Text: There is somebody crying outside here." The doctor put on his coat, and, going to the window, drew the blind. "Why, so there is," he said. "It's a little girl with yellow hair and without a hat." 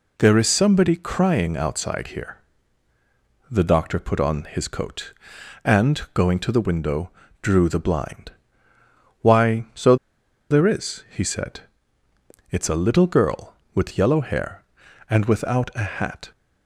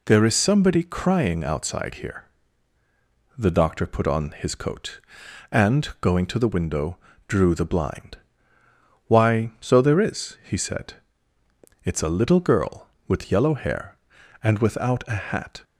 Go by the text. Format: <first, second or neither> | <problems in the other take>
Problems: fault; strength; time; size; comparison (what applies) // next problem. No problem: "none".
second | pauses between "so" and "there"; noticeable; at 9.9 s; 0.54 s long